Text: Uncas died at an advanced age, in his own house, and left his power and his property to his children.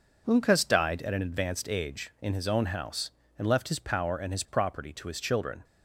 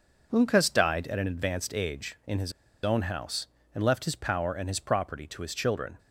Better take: first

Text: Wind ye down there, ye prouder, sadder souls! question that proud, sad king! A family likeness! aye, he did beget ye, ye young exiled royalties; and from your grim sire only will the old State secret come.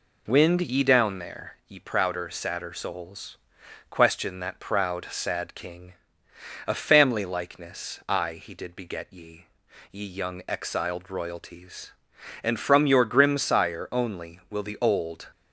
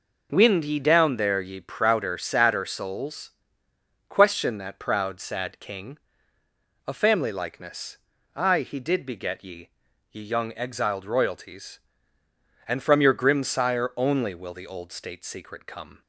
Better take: second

